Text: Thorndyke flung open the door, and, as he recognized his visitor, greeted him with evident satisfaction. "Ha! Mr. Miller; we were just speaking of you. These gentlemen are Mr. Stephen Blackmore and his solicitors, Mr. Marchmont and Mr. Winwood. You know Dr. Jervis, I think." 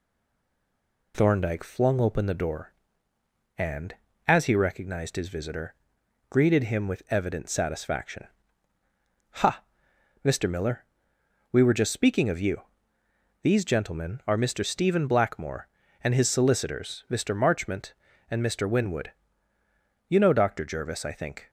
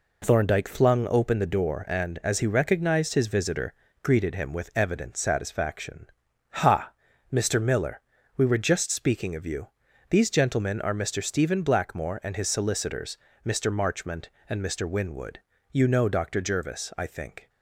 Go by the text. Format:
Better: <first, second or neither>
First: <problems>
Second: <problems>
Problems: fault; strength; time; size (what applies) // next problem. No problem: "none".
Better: second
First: stays silent before the first word; until 1.1 s; 1.1 s long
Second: none